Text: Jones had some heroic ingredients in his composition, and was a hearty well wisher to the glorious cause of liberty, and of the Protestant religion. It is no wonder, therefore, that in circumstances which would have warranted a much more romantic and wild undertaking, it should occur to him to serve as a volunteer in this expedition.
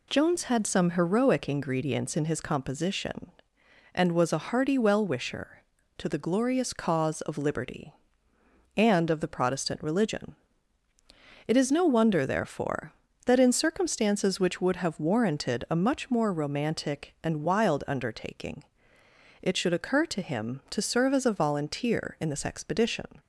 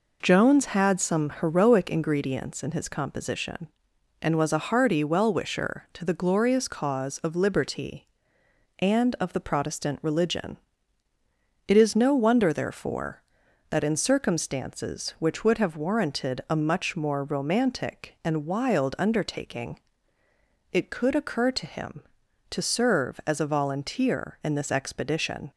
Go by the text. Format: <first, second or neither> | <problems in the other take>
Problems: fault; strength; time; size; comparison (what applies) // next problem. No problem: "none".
first | says "could" for "should"; at 20.9 s